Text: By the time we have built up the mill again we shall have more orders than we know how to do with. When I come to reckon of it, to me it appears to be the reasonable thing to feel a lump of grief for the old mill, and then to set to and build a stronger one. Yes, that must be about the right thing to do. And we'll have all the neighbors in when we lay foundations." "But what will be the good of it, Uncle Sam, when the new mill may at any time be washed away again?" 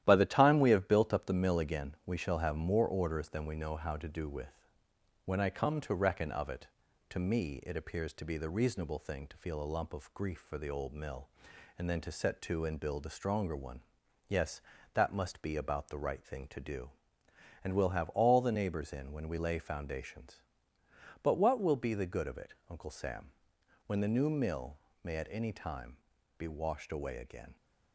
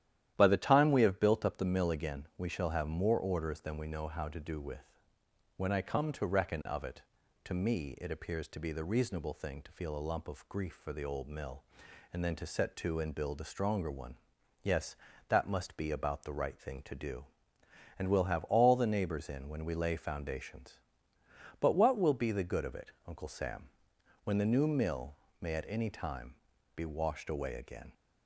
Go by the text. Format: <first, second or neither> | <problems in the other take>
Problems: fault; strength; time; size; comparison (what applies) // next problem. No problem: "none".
second | gets quieter; noticeable; throughout; 5.5 dB // starts louder than the rest; strong; until 1.0 s; 12 dB; strong in the second // pauses between "mill" and "may"; slight; at 24.7 s; 0.26 s long; slight in the second // pauses between "time" and "be"; at 25.9 s; 0.40 s long; also in the second